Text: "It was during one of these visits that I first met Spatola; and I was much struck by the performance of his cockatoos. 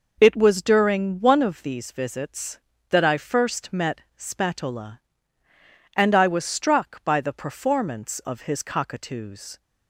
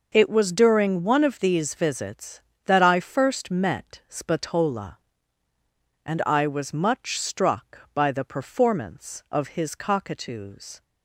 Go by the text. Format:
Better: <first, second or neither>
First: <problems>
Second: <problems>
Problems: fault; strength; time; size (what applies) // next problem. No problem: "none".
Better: second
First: pauses between "met" and "Spatola"; slight; at 4.0 s; 0.16 s long // skips "much"; at 6.4 s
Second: none